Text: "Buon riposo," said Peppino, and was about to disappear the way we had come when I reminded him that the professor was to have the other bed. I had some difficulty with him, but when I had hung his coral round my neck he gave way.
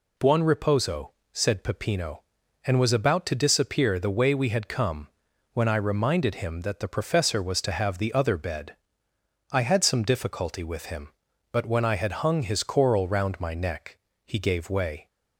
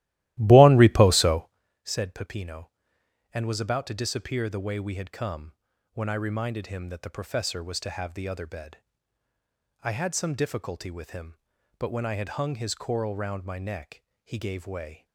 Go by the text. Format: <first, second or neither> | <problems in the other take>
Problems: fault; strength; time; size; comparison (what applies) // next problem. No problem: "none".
first | starts louder than the rest; strong; until 1.6 s; 16 dB // pauses between "come" and "when"; at 5.5 s; 0.42 s long; also in the first // pauses between "neck" and "he"; slight; at 14.0 s; 0.22 s long; slight in the first